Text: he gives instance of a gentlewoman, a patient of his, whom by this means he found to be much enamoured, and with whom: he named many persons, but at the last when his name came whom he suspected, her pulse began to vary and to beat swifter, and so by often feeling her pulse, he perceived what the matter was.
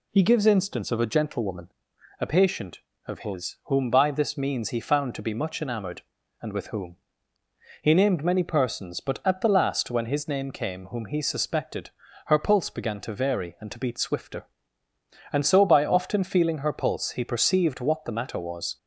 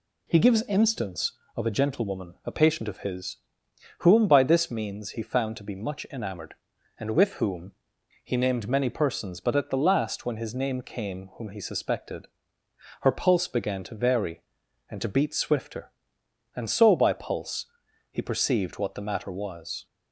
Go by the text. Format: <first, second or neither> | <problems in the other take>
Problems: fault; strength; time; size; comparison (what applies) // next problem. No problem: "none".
first | skips "often feeling her"; at 17.1 s